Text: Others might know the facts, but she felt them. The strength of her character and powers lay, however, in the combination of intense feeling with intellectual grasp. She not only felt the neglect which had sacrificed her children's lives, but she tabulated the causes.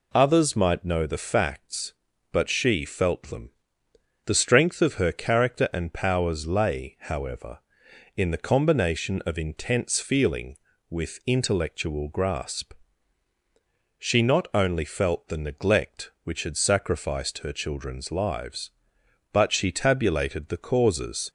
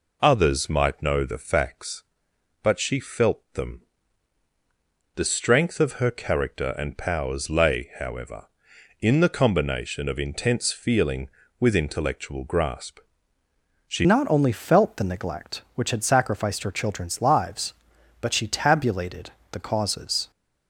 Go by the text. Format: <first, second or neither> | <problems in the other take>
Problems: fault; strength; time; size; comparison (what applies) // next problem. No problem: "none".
first | changes voice at "not"; from 14.0 s on; 6.3 s long // pauses between "tabulated" and "the"; slight; at 19.3 s; 0.20 s long